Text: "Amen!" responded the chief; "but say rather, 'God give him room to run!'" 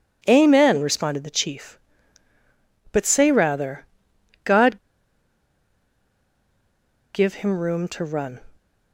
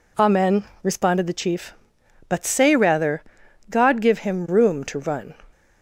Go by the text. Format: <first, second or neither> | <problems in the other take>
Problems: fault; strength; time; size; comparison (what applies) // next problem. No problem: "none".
second | pauses between "God" and "give"; strong; at 4.7 s; 2.3 s long